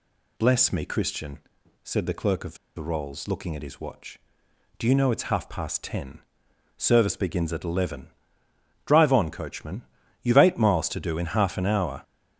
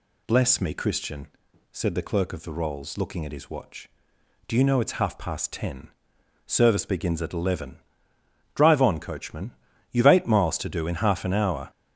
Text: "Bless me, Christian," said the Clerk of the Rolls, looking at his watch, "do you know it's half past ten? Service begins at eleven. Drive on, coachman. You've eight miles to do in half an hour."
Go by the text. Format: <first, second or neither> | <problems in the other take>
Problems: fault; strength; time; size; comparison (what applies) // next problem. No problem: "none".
second | pauses between "of" and "the"; slight; at 2.5 s; 0.20 s long